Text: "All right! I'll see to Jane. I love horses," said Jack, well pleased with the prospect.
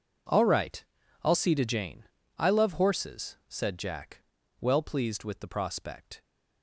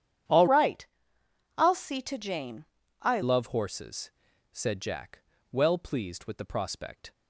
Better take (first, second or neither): first